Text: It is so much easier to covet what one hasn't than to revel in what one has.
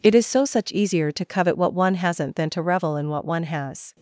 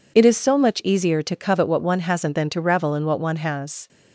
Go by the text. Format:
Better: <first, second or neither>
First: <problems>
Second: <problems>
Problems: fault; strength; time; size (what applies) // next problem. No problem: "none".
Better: second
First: says "such" for "much"; at 0.4 s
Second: none